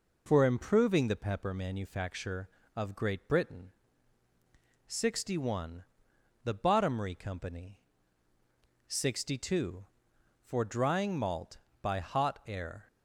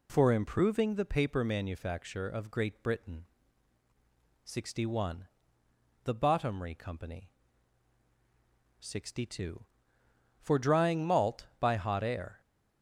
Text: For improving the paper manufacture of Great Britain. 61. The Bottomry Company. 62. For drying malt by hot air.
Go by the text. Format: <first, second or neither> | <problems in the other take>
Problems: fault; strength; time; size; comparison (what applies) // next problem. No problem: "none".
second | says "pepper" for "paper"; at 1.1 s